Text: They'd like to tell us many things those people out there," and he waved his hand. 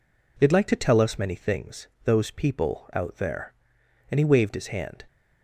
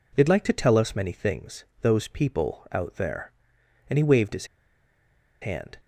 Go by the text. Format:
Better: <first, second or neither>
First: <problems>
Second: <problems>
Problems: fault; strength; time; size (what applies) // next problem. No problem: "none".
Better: first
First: pauses between "things" and "those"; slight; at 1.8 s; 0.18 s long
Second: pauses between "things" and "those"; slight; at 1.6 s; 0.18 s long // pauses between "his" and "hand"; noticeable; at 4.4 s; 0.95 s long